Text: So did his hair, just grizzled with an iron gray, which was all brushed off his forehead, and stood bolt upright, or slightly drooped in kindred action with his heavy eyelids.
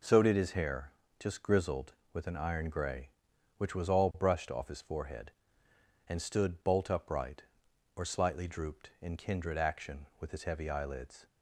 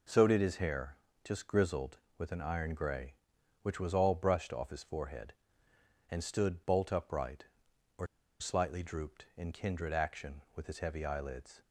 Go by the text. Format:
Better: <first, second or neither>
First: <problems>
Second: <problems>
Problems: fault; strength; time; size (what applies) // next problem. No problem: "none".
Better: first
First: none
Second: pauses between "or" and "slightly"; slight; at 8.0 s; 0.34 s long